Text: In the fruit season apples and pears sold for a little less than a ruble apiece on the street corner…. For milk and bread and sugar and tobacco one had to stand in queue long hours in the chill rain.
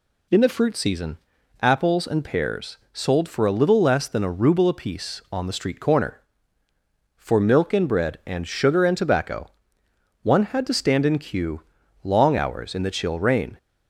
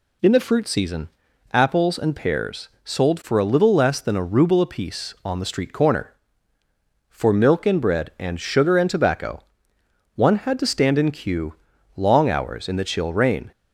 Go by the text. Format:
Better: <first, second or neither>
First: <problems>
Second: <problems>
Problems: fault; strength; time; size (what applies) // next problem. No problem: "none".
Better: neither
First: pauses between "season" and "apples"; noticeable; at 1.1 s; 0.46 s long // pauses between "pears" and "sold"; slight; at 2.7 s; 0.16 s long // pauses between "tobacco" and "one"; noticeable; at 9.5 s; 0.72 s long // pauses between "queue" and "long"; at 11.6 s; 0.42 s long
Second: pauses between "season" and "apples"; noticeable; at 1.0 s; 0.46 s long // pauses between "pears" and "sold"; slight; at 2.6 s; 0.16 s long // pauses between "tobacco" and "one"; noticeable; at 9.4 s; 0.72 s long // pauses between "queue" and "long"; at 11.5 s; 0.42 s long